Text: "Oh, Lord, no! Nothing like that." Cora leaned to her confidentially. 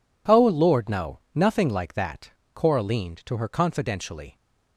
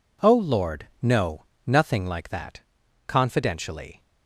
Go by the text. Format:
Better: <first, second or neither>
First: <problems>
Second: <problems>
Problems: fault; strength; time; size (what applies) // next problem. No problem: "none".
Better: first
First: none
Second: skips "Cora leaned to her"; at 2.8 s